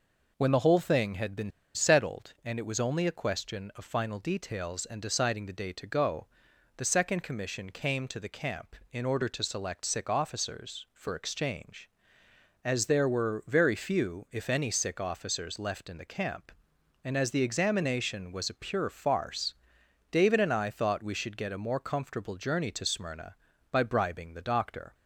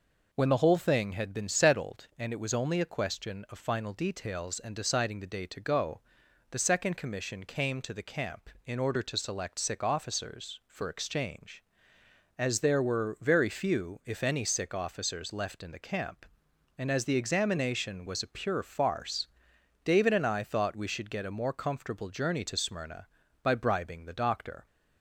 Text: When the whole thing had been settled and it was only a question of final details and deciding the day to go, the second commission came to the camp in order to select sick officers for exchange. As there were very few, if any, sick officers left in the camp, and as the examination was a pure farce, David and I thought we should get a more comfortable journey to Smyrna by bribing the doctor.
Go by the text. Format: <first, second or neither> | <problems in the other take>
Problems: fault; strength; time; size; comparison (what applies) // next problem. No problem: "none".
second | pauses between "been" and "settled"; slight; at 1.5 s; 0.25 s long